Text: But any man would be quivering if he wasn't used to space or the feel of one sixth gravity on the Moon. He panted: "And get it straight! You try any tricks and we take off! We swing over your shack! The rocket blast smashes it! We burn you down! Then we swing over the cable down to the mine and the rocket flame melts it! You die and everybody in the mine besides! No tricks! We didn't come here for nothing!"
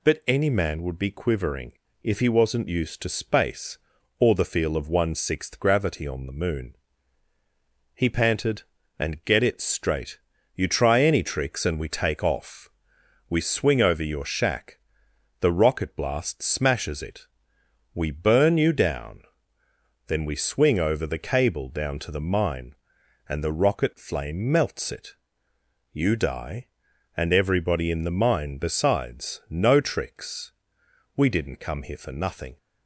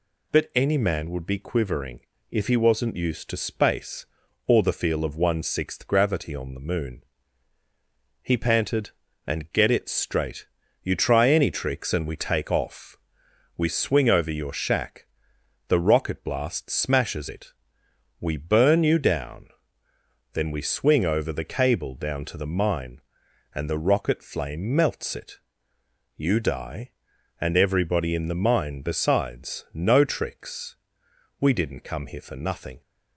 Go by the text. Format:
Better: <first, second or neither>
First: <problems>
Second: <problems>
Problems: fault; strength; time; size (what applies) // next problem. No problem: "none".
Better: neither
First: pauses between "quivering" and "if"; slight; at 1.7 s; 0.30 s long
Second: pauses between "quivering" and "if"; slight; at 2.0 s; 0.30 s long